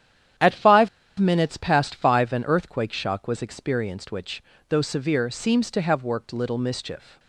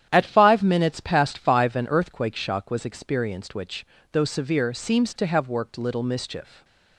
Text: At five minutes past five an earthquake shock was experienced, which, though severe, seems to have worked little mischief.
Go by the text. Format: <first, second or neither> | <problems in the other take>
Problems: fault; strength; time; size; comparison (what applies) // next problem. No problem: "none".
second | starts louder than the rest; strong; until 1.7 s; 10 dB; strong in the second // pauses between "five" and "minutes"; slight; at 0.8 s; 0.30 s long